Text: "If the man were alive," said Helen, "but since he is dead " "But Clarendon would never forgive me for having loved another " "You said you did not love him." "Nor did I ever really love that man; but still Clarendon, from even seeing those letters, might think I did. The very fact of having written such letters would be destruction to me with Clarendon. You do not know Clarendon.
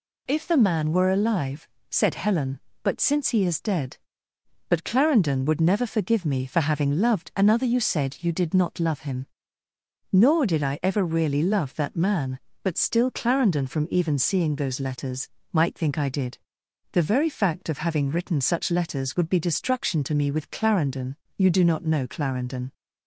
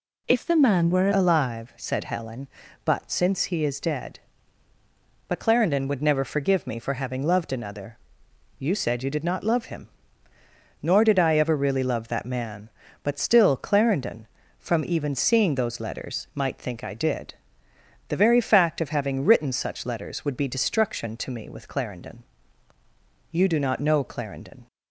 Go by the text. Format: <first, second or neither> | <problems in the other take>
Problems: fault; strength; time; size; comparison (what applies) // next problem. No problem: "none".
first | changes voice at "alive"; from 1.1 s on; 23.5 s long